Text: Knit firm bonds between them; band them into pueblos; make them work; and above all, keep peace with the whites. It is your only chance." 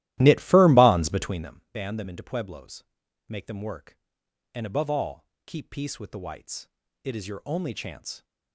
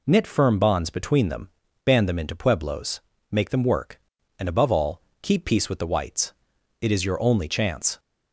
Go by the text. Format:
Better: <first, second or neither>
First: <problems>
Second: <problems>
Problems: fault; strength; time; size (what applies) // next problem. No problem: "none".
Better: second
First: starts louder than the rest; strong; until 1.5 s; 15 dB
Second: none